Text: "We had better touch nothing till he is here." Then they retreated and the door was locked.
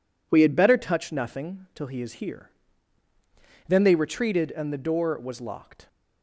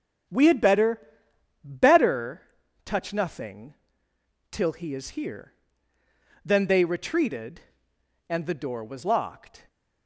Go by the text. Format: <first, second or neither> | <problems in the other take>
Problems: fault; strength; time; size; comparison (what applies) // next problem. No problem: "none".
first | starts louder than the rest; until 1.9 s; 7 dB // says "better" twice; at 1.6 s // pauses between "nothing" and "till"; noticeable; at 3.7 s; 0.78 s long